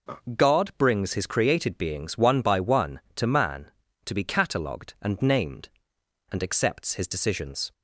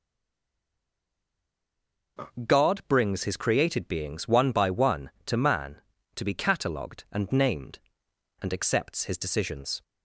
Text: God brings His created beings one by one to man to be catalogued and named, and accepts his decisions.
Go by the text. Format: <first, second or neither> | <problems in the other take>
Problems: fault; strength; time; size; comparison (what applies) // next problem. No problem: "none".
first | stays silent before the first word; until 2.1 s; 2.1 s long // starts louder than the rest; noticeable; until 3.5 s; 6 dB; noticeable in the first